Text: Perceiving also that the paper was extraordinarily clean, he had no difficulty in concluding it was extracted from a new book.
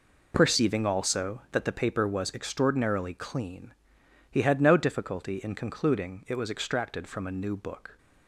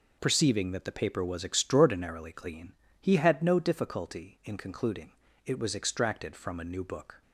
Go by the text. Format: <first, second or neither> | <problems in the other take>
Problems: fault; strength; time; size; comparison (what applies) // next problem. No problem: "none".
first | skips "also"; at 0.7 s // pauses between "concluding" and "it"; slight; at 5.1 s; 0.32 s long